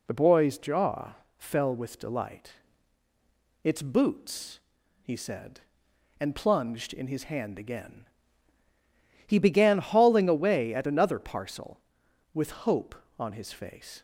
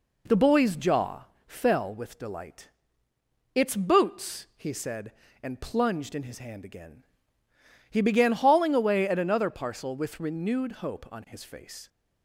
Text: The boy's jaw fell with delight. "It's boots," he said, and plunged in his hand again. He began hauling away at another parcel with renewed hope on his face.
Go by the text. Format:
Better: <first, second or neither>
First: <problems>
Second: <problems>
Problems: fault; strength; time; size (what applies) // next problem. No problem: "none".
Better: second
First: pauses between "jaw" and "fell"; slight; at 1.1 s; 0.24 s long // skips "renewed"; at 12.6 s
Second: pauses between "jaw" and "fell"; slight; at 1.2 s; 0.20 s long